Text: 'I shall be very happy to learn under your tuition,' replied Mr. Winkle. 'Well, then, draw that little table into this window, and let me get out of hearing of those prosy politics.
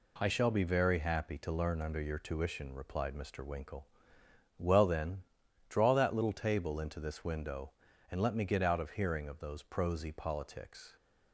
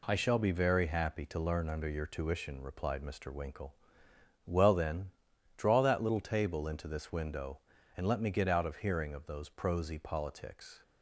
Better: neither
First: none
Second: none

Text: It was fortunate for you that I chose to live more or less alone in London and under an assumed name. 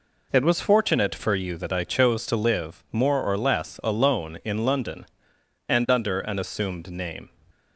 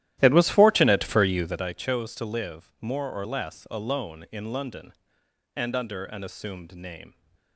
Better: first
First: none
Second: starts louder than the rest; strong; until 1.7 s; 13.5 dB

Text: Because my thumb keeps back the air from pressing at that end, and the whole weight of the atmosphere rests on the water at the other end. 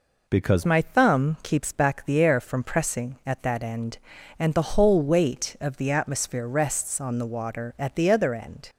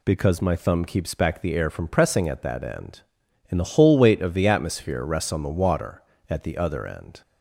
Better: second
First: changes voice at "my"; from 0.6 s on; 8.0 s long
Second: none

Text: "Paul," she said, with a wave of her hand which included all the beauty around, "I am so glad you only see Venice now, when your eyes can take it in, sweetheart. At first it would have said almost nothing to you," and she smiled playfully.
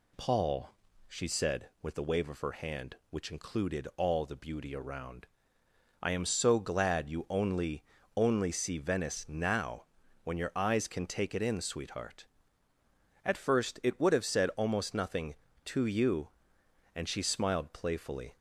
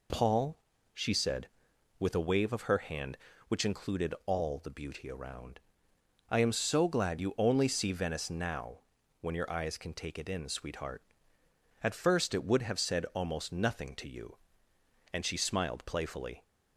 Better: second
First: says "only" twice; at 8.1 s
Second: none

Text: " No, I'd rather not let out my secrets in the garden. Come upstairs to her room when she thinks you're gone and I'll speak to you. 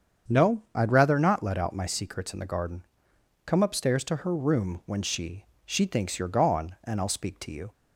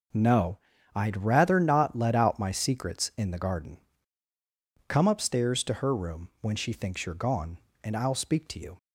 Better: second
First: starts louder than the rest; strong; until 1.3 s; 7.5 dB // says "she" twice; at 5.6 s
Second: none

